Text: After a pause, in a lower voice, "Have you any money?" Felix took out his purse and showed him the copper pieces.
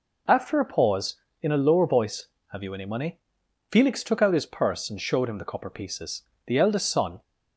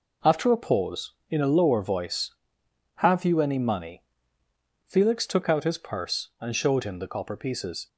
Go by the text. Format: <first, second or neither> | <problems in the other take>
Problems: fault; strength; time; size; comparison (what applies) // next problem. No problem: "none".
second | goes on to say "The eldest son"; noticeable; from 6.4 s on; 0.76 s long